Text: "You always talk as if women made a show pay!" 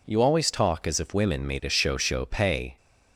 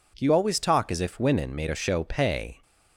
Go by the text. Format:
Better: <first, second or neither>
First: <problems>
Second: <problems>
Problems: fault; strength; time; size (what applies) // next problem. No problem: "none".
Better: second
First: says "show" twice; at 1.9 s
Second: none